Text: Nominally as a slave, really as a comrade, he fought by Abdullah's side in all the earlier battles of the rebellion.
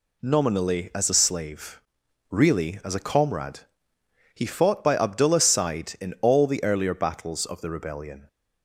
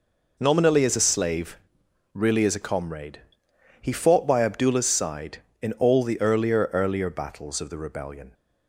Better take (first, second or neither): first